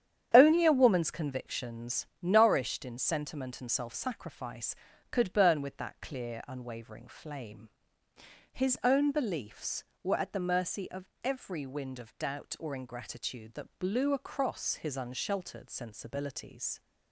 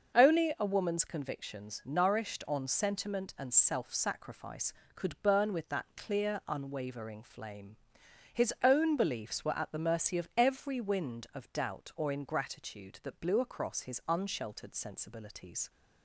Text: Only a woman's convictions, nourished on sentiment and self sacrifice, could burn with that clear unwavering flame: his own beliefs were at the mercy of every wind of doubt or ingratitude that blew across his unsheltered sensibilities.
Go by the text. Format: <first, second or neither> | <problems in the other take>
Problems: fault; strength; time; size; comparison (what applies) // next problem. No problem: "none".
second | starts louder than the rest; strong; until 1.3 s; 9 dB; also in the second // says "in" for "on"; at 2.8 s // pauses between "of" and "every"; slight; at 11.0 s; 0.18 s long